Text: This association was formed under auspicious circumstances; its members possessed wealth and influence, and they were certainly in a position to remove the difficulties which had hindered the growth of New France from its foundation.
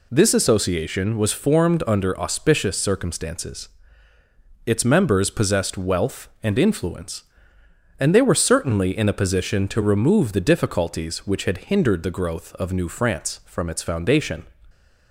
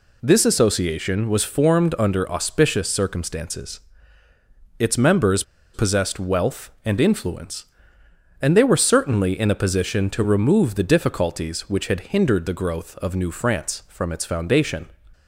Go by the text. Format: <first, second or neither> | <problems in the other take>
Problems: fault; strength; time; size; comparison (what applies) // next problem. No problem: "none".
first | pauses between "members" and "possessed"; slight; at 5.4 s; 0.31 s long